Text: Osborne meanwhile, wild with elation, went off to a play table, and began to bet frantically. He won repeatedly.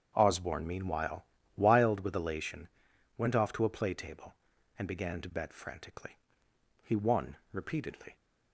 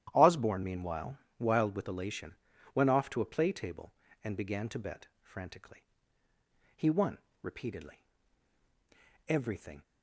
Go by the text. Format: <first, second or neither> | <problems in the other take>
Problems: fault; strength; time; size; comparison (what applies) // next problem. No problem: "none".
first | starts louder than the rest; strong; until 1.1 s; 11.5 dB; strong in the first // pauses between "won" and "repeatedly"; slight; at 7.1 s; 0.24 s long; slight in the first // goes on to say "Everything"; from 9.2 s on; 0.56 s long